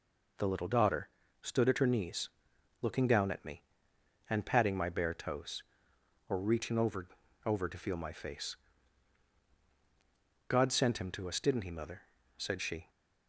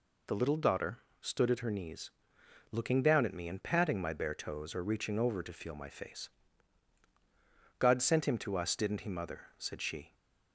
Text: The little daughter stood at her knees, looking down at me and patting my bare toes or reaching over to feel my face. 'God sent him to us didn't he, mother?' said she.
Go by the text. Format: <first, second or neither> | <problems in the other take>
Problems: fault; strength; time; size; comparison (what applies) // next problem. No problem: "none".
second | pauses between "daughter" and "stood"; slight; at 1.0 s; 0.34 s long; slight in the second // says "over" twice; at 7.4 s